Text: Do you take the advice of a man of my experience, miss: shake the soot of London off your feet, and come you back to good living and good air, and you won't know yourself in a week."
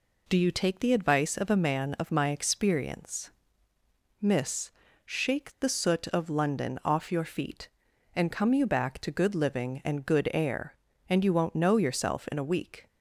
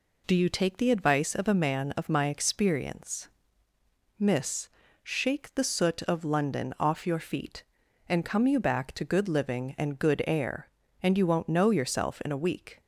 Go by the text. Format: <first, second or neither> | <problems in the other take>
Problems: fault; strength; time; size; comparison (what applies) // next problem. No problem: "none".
neither | none